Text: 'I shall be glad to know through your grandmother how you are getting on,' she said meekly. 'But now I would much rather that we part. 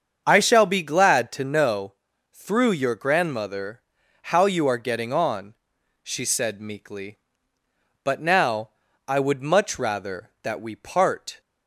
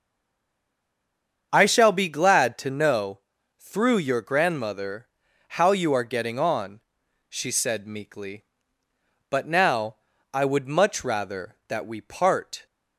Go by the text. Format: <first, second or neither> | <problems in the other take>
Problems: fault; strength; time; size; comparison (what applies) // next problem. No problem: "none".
first | stays silent before the first word; noticeable; until 1.5 s; 1.5 s long // starts louder than the rest; strong; until 2.5 s; 7.5 dB; strong in the first // pauses between "know" and "through"; at 3.1 s; 0.38 s long; also in the first // pauses between "grandmother" and "how"; at 5.0 s; 0.42 s long; also in the first // pauses between "now" and "I"; at 9.9 s; 0.38 s long; also in the first